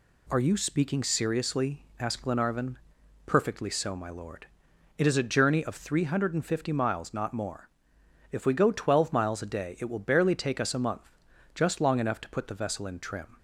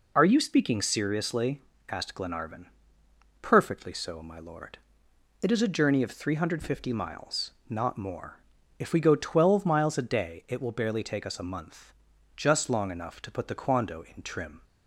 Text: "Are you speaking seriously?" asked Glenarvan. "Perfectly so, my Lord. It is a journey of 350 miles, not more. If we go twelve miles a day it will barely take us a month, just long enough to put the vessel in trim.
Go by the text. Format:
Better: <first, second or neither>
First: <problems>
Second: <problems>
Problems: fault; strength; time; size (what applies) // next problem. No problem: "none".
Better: first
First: none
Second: says "quando" for "vessel"; at 13.6 s